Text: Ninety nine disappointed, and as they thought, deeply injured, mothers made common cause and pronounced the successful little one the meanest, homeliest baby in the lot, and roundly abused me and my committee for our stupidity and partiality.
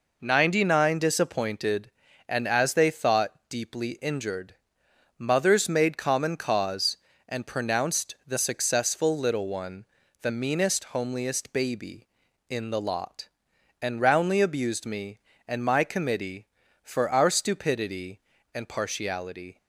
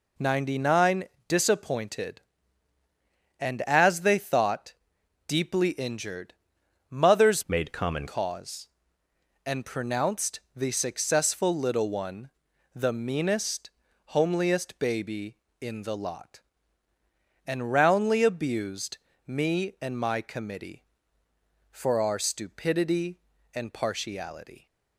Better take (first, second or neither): first